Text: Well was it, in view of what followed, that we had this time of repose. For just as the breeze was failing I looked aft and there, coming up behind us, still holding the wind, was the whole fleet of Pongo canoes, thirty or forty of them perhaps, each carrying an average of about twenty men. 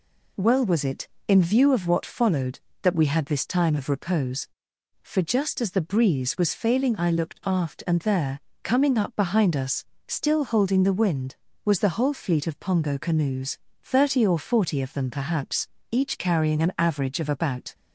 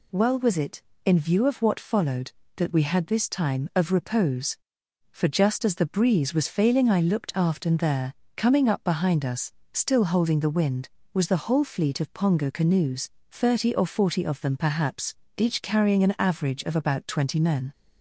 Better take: second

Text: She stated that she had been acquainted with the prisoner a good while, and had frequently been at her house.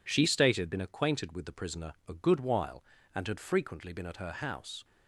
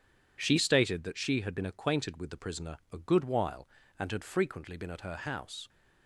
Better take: second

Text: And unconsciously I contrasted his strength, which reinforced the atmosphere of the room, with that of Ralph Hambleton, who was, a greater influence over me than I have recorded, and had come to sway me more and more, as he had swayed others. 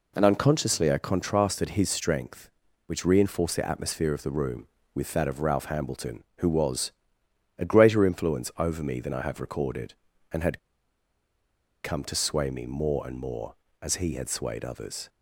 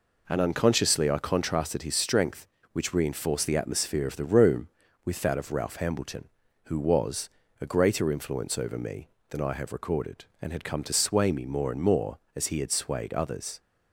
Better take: second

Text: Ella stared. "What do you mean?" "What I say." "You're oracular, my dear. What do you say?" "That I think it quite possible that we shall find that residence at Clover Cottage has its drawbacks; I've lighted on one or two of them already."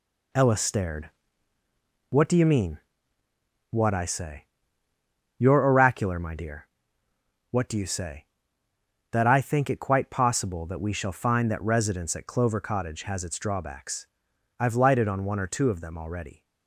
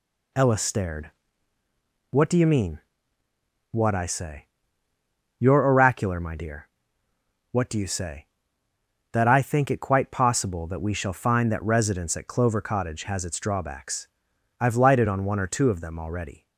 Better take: second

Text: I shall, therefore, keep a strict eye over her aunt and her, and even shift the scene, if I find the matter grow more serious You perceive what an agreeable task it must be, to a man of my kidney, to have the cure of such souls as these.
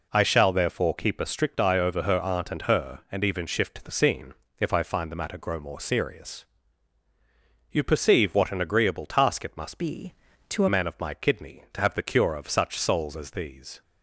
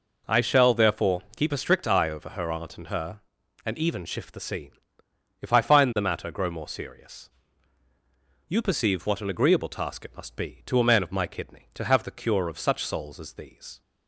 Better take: second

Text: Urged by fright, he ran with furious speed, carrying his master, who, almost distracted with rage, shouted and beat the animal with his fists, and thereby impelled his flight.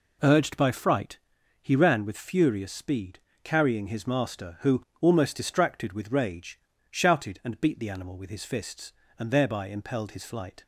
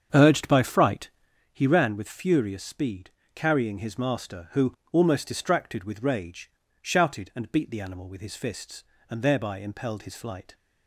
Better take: first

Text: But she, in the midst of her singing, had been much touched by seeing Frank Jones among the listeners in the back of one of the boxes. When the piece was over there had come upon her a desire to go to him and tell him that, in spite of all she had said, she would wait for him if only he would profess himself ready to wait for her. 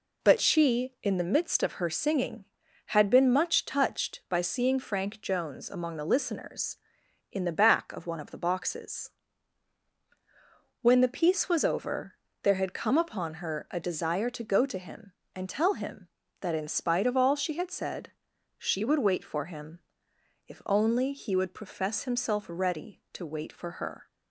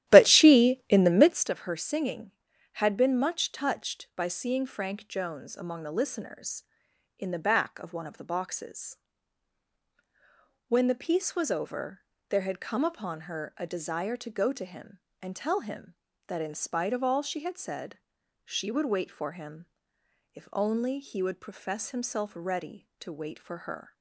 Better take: first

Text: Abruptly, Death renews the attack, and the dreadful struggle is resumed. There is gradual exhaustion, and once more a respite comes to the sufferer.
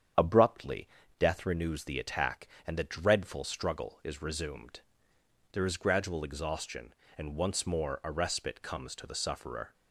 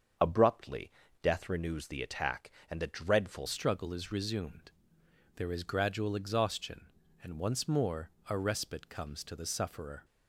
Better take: first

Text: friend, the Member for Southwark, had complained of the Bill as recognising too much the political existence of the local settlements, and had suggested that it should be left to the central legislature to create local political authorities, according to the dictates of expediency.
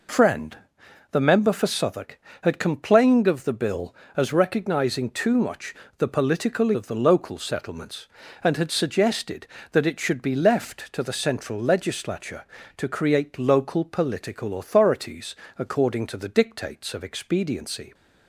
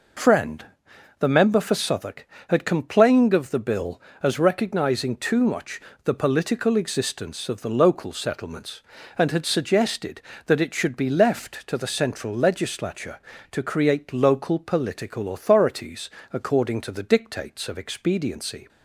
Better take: second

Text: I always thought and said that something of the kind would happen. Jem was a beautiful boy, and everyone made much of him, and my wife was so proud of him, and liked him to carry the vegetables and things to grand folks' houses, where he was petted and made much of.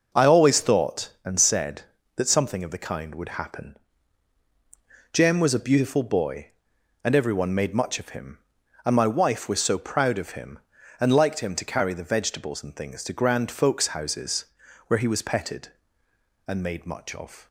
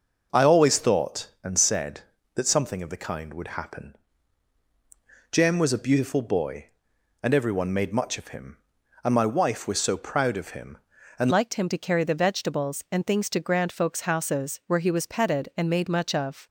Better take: first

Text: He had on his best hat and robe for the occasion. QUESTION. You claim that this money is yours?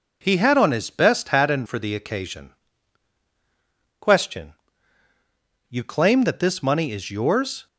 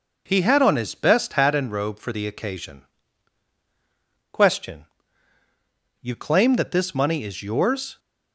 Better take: second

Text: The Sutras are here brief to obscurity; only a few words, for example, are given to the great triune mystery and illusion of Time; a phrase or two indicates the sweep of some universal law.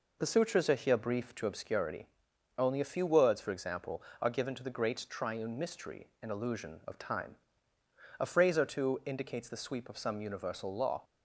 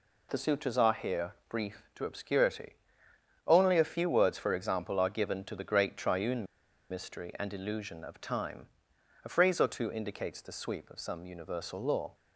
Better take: first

